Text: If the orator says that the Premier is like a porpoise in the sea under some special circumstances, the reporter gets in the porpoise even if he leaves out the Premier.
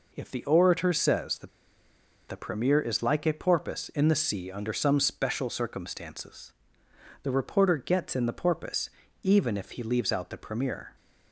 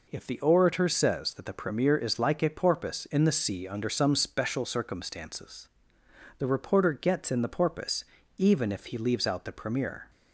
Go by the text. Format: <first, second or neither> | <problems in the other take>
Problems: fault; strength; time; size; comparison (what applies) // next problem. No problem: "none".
second | pauses between "that" and "the"; noticeable; at 1.4 s; 0.79 s long // pauses between "porpoise" and "even"; slight; at 8.8 s; 0.32 s long; slight in the second